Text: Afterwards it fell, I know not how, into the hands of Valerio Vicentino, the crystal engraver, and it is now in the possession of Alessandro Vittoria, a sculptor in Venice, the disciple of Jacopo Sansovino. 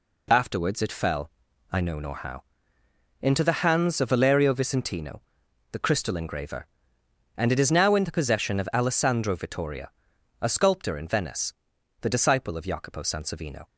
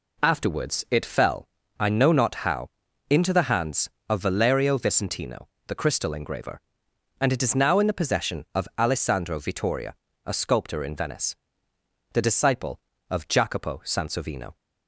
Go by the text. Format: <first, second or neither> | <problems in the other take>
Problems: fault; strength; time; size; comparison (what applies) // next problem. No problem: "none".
second | says "nor" for "not"; at 1.9 s